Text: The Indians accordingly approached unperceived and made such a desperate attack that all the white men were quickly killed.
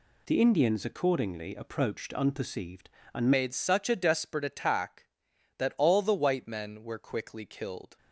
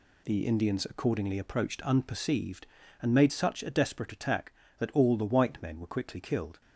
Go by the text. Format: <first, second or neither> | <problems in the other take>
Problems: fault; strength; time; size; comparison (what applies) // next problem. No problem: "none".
second | changes voice at "made"; from 3.3 s on; 4.6 s long